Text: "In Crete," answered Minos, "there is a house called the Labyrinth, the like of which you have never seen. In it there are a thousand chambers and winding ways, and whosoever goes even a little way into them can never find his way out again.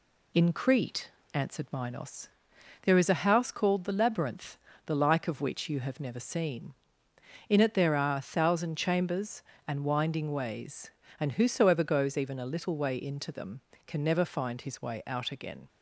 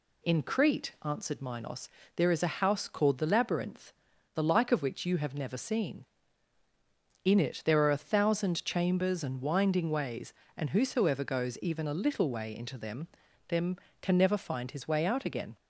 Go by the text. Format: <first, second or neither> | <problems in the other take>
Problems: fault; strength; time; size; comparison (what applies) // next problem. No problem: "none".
first | says "them" twice; at 13.4 s